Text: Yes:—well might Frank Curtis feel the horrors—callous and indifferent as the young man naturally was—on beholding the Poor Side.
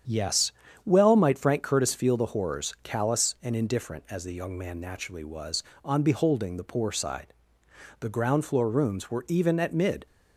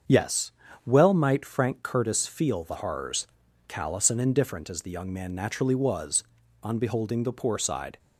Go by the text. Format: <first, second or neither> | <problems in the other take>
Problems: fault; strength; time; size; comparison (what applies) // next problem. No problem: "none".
second | starts louder than the rest; strong; until 1.4 s; 8.5 dB; also in the second // goes on to say "The ground floor rooms were even at mid"; strong; from 7.9 s on; 2.0 s long